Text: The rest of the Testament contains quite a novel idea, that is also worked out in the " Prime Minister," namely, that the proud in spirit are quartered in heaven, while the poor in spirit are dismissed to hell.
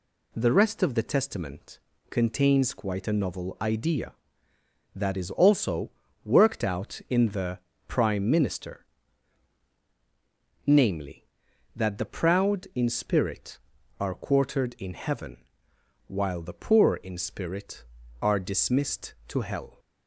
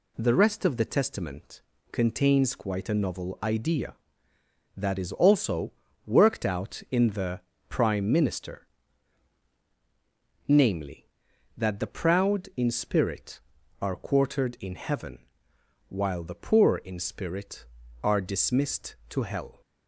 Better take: neither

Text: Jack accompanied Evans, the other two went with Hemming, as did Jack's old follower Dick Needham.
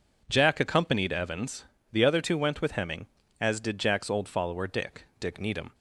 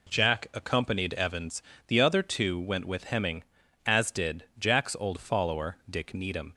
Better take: second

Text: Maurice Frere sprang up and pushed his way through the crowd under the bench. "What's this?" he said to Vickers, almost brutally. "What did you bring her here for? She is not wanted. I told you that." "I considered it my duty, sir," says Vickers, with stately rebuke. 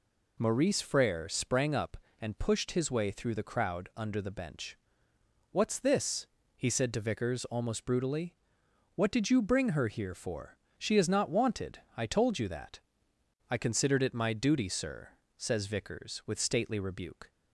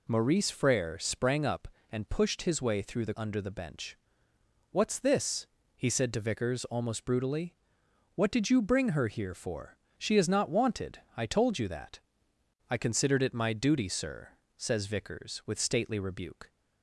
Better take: first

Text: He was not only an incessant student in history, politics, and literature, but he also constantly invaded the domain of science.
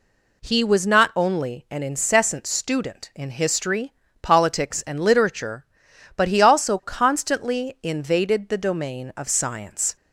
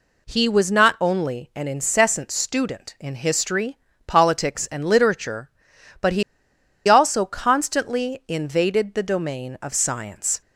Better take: first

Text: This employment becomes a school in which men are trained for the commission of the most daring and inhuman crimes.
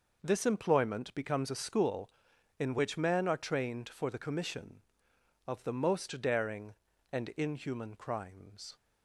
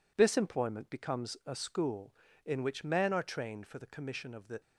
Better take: first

